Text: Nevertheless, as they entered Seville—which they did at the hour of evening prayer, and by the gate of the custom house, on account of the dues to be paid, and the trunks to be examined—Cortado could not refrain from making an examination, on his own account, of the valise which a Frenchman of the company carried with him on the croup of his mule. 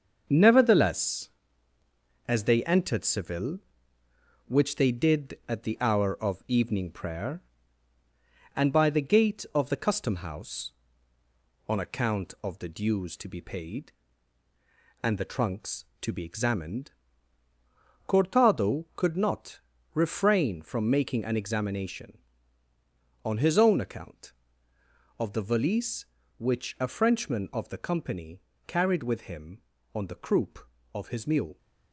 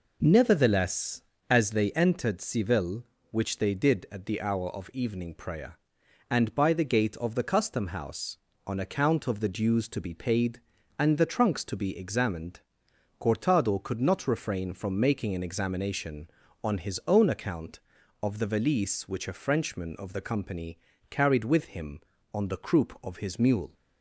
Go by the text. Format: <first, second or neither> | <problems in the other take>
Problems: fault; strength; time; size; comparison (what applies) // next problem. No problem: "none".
second | gets quieter; noticeable; throughout; 6 dB // pauses between "not" and "refrain"; slight; at 19.5 s; 0.34 s long // pauses between "company" and "carried"; slight; at 28.3 s; 0.28 s long; slight in the second